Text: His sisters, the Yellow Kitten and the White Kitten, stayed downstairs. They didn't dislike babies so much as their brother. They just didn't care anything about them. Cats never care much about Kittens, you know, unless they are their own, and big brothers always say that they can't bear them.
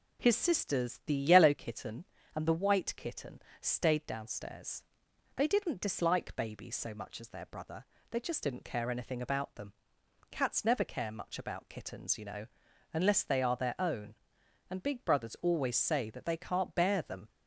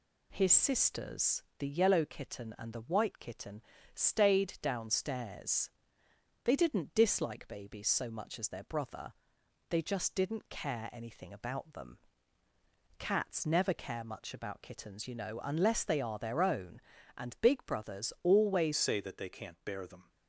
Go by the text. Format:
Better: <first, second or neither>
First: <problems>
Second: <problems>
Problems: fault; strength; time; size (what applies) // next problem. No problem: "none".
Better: first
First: none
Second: changes voice at "say"; from 18.7 s on; 1.3 s long